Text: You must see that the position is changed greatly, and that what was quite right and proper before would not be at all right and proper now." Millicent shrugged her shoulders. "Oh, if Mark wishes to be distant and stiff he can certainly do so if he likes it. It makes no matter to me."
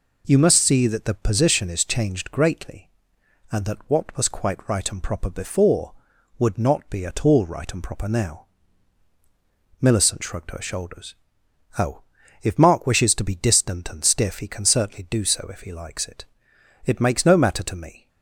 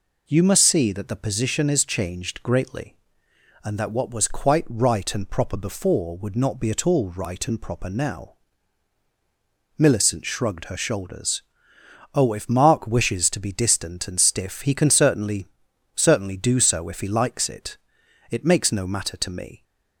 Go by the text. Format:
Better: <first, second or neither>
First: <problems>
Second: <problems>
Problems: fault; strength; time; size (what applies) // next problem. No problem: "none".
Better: first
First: none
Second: says "certainly" twice; at 15.9 s